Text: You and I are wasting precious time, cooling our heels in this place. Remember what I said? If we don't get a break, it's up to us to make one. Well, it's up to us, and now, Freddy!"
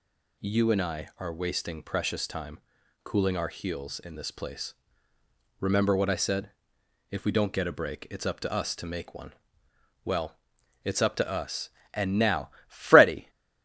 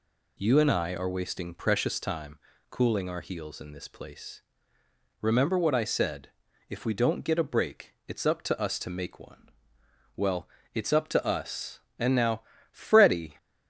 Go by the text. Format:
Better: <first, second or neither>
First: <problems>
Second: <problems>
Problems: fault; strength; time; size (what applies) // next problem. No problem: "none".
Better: neither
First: none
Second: none